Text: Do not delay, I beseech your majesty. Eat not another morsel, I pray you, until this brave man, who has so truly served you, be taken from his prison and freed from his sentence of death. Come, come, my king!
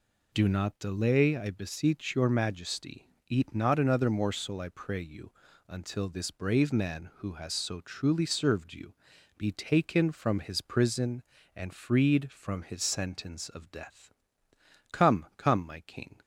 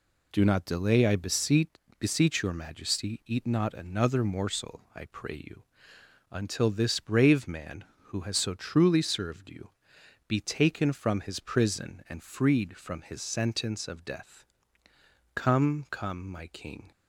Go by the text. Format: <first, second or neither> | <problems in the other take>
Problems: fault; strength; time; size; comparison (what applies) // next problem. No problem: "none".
first | says "beseech" twice; at 1.9 s